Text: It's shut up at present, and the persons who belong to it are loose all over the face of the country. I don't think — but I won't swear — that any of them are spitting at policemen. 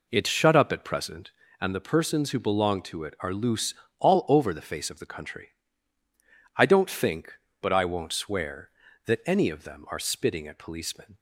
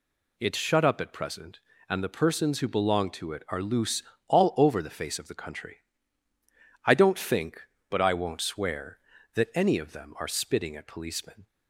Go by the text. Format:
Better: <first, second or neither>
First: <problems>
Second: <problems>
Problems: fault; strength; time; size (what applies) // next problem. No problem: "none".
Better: second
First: starts louder than the rest; until 1.5 s; 4 dB // pauses between "loose" and "all"; slight; at 3.7 s; 0.26 s long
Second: pauses between "loose" and "all"; slight; at 4.0 s; 0.26 s long